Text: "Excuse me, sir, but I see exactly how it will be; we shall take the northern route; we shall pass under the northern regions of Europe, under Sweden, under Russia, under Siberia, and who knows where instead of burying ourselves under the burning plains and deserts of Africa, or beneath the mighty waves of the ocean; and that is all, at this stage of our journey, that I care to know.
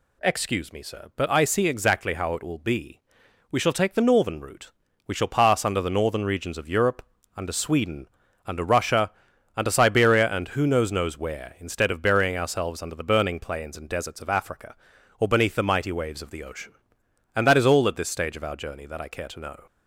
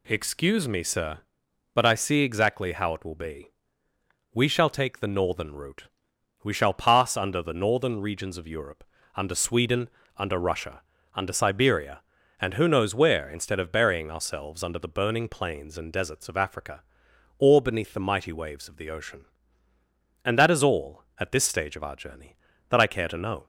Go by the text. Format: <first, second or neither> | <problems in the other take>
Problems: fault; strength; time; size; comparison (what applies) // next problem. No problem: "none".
second | says "knows" twice; at 10.8 s